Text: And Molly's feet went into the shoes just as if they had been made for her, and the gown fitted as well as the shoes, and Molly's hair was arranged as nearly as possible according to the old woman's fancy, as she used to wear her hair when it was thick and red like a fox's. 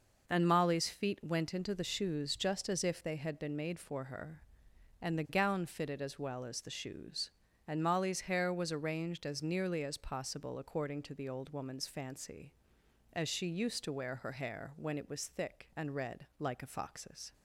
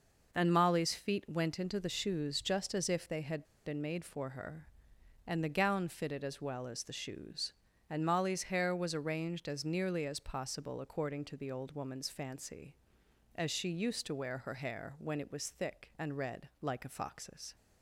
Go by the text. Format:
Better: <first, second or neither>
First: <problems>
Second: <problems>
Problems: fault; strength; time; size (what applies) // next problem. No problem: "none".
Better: first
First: none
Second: pauses between "had" and "been"; slight; at 3.4 s; 0.22 s long